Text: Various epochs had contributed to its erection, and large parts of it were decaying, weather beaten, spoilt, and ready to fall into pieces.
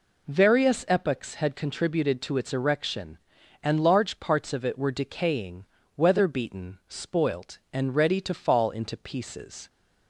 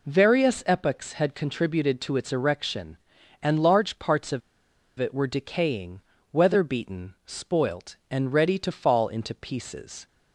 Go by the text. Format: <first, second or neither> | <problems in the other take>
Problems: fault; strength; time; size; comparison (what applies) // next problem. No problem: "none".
first | pauses between "of" and "it"; noticeable; at 4.4 s; 0.58 s long